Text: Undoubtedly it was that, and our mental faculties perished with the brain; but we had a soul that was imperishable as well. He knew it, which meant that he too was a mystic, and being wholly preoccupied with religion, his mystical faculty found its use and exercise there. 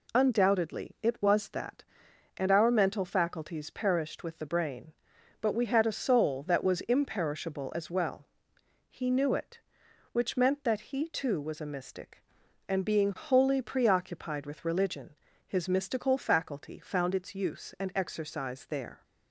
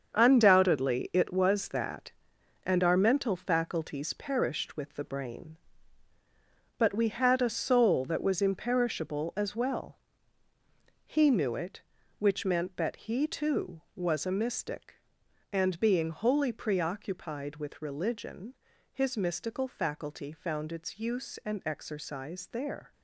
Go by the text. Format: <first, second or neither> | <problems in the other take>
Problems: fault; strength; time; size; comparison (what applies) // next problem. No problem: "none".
first | gets quieter; strong; throughout; 9.5 dB